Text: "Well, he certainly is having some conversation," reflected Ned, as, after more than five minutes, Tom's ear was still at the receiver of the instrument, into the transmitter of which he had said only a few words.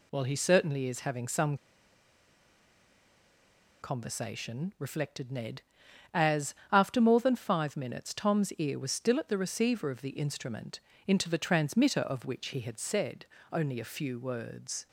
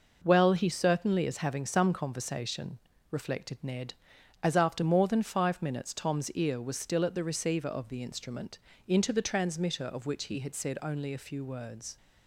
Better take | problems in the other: second | pauses between "some" and "conversation"; strong; at 1.5 s; 2.2 s long // pauses between "said" and "only"; slight; at 13.2 s; 0.26 s long

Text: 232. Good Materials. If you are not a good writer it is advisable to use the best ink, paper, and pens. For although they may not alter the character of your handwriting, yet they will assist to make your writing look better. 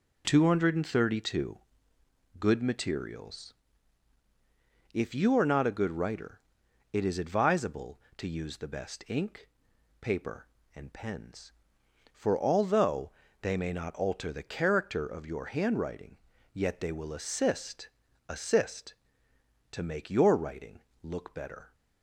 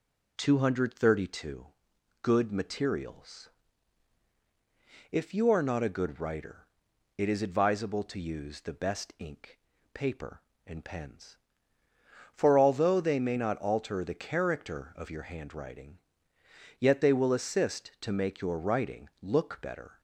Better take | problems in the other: second | pauses between "writer" and "it"; noticeable; at 6.3 s; 0.52 s long; noticeable in the second // pauses between "although" and "they"; slight; at 13.1 s; 0.32 s long // says "assist" twice; at 18.2 s // pauses between "writing" and "look"; slight; at 20.8 s; 0.22 s long

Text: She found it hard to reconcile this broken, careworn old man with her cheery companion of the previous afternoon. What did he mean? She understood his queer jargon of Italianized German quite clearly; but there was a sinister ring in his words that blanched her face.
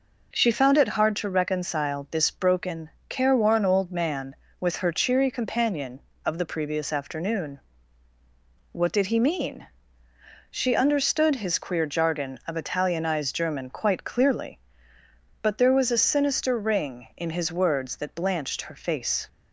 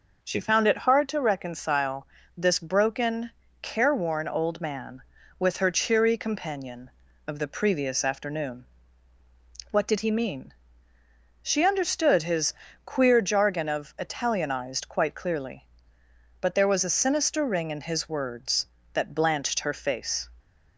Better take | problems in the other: first | pauses between "reconcile" and "this"; slight; at 2.0 s; 0.30 s long // pauses between "his" and "queer"; slight; at 12.5 s; 0.32 s long // skips "German"; at 14.8 s

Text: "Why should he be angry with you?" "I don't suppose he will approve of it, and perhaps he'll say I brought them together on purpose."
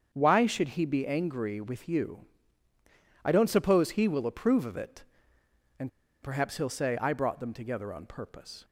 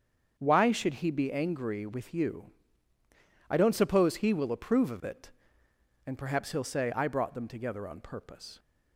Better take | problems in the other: second | starts louder than the rest; strong; until 1.1 s; 7 dB; strong in the second // pauses between "and" and "perhaps"; slight; at 5.8 s; 0.34 s long

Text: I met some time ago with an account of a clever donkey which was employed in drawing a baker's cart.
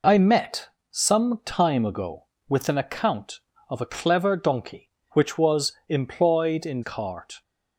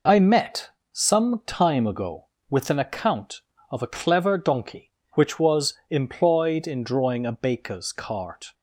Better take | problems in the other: second | pauses between "met" and "some"; slight; at 0.6 s; 0.24 s long; slight in the second // pauses between "was" and "employed"; slight; at 5.7 s; 0.16 s long; slight in the second // skips "drawing a baker's"; at 6.8 s

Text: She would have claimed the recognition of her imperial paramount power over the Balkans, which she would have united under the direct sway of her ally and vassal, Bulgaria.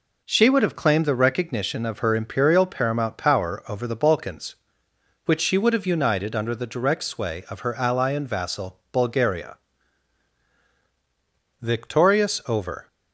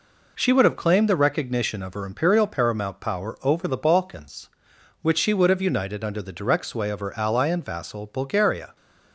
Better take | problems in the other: second | goes on to say "Victorious over"; noticeable; from 11.6 s on; 1.2 s long

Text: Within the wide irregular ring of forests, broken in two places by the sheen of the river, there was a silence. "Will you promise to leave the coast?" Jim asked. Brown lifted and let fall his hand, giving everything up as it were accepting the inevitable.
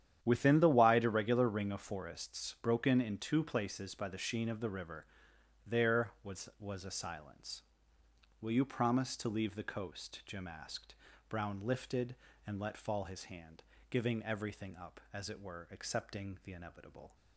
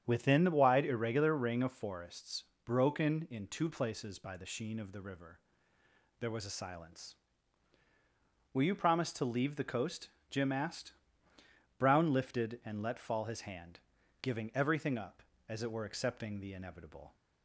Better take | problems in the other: second | starts louder than the rest; strong; until 1.2 s; 10 dB; strong in the second // says "was" twice; at 6.5 s

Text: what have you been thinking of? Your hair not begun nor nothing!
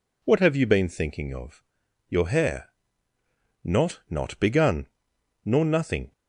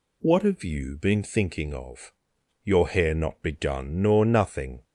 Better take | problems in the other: second | pauses between "hair" and "not"; noticeable; at 2.6 s; 0.96 s long // says "not" twice; at 4.1 s // pauses between "begun" and "nor"; noticeable; at 4.8 s; 0.58 s long

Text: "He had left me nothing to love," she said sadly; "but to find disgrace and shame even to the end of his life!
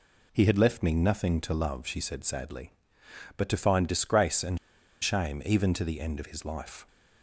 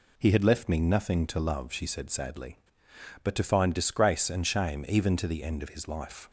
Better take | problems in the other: second | pauses between "and" and "shame"; at 4.5 s; 0.44 s long

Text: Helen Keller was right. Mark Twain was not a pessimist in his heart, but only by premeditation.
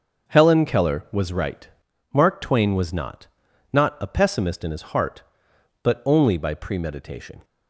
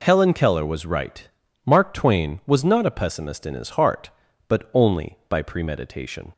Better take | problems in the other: second | starts louder than the rest; until 1.3 s; 7 dB // says "not" twice; at 3.7 s

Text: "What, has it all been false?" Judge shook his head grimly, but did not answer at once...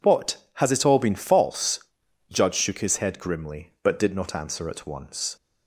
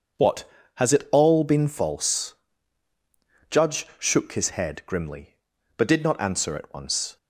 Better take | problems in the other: neither | none

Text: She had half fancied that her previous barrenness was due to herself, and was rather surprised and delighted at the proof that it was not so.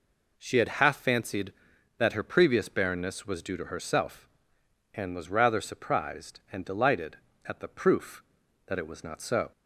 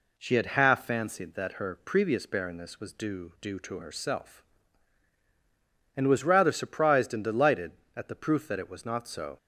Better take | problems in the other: first | says "due" twice; at 3.3 s

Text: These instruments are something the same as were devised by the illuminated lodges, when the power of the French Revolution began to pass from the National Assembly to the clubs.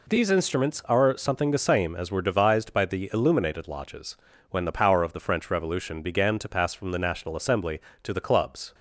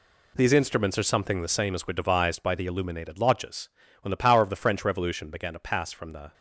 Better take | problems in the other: first | stops before "National Assembly to the clubs"; at 6.3 s

